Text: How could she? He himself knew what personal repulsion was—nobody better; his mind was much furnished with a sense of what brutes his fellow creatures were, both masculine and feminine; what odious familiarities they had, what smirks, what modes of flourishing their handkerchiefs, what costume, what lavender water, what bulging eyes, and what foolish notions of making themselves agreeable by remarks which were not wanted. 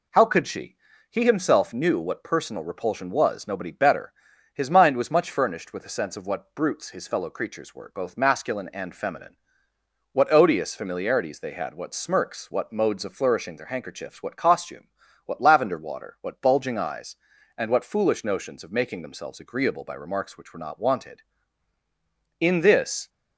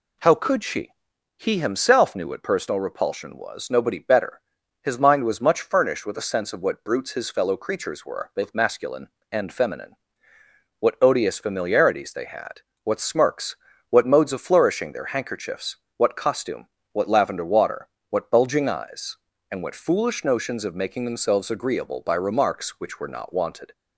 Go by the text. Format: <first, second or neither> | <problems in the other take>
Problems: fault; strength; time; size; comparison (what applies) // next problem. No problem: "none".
second | goes on to say "In this"; noticeable; from 22.3 s on; 0.70 s long